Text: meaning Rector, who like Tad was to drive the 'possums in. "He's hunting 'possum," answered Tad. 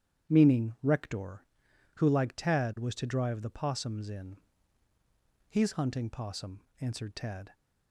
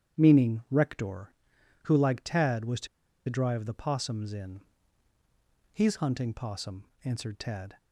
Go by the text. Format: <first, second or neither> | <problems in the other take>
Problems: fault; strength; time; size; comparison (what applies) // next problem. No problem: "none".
first | starts louder than the rest; strong; until 1.2 s; 9.5 dB; strong in the first // pauses between "to" and "drive"; at 2.8 s; 0.41 s long